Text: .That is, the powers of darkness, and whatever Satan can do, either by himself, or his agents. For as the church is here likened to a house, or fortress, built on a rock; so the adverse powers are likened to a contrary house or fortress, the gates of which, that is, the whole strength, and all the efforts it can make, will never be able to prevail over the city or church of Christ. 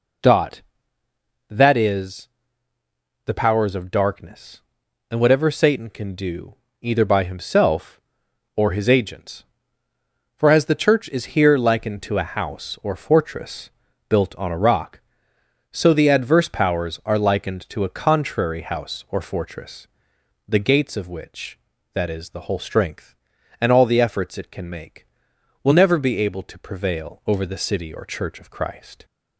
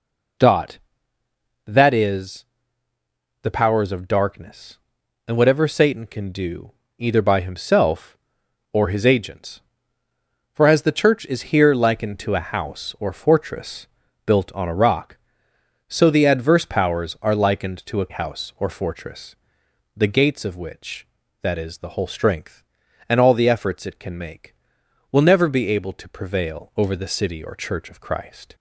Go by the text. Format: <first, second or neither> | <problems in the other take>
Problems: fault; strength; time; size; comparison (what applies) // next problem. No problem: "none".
first | skips "contrary"; at 18.1 s